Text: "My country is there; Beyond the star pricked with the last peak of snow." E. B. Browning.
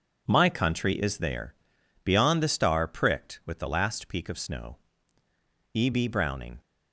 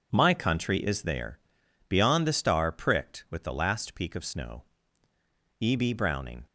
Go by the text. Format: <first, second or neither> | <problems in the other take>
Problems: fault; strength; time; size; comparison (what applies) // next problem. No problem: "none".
neither | none